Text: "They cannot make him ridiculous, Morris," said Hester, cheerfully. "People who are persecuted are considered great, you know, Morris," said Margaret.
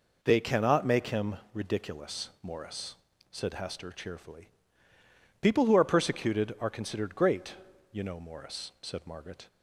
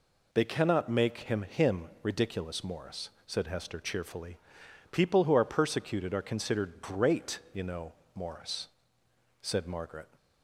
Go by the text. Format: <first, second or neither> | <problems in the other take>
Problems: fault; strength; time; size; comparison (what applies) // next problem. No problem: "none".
first | says "him" twice; at 1.4 s